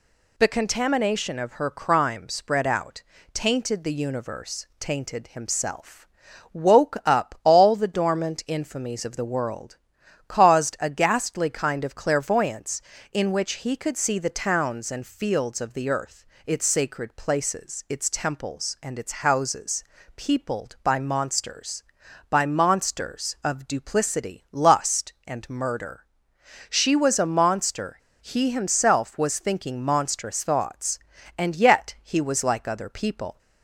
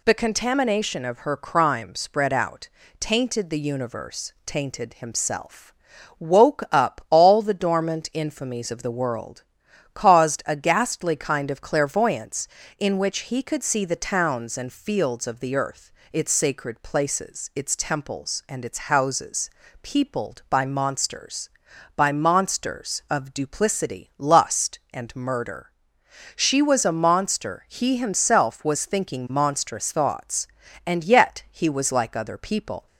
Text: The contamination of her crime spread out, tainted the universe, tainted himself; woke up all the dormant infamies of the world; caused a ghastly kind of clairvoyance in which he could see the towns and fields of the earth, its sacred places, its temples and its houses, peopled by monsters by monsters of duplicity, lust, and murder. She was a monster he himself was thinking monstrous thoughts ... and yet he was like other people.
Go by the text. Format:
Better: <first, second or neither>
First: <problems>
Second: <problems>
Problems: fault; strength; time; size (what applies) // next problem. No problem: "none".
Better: second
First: pauses between "monster" and "he"; slight; at 27.9 s; 0.22 s long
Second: none